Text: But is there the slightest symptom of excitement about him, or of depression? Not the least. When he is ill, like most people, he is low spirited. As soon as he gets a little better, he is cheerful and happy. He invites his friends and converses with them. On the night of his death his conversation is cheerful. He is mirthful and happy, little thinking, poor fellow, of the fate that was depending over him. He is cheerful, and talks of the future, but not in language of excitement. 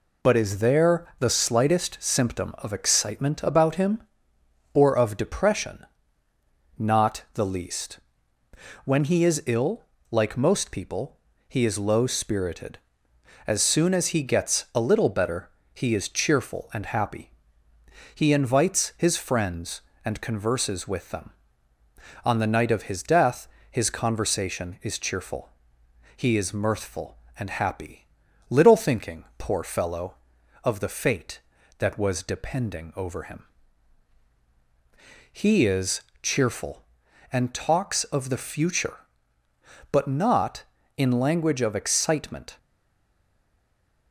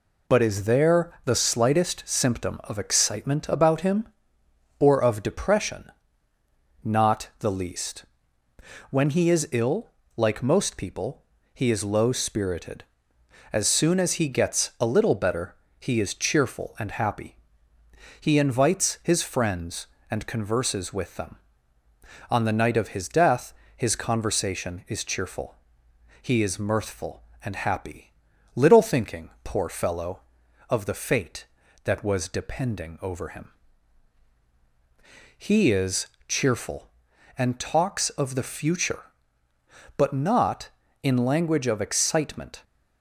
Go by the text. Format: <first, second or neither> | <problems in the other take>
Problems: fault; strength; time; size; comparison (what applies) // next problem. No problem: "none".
second | pauses between "death" and "his"; slight; at 23.4 s; 0.22 s long; slight in the second // pauses between "is" and "cheerful"; slight; at 36.0 s; 0.20 s long; slight in the second // stays silent after the last word; noticeable; from 42.5 s on; 1.6 s long